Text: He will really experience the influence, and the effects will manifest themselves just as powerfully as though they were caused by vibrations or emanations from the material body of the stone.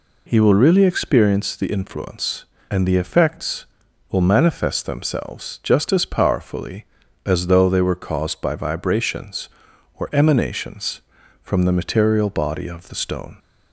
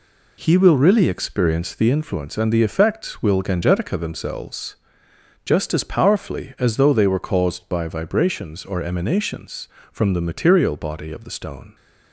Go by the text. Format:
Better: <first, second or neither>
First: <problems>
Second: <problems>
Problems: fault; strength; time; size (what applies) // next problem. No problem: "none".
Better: first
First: none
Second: says "gangetica" for "manifest"; at 3.4 s // pauses between "themselves" and "just"; noticeable; at 4.7 s; 0.66 s long